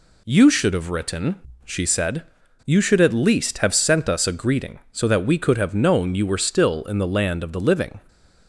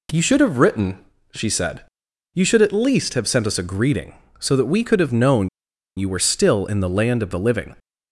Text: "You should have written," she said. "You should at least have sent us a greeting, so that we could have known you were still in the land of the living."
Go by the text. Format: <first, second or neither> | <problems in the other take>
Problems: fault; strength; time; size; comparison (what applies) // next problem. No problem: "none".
first | pauses between "known" and "you"; noticeable; at 5.4 s; 0.49 s long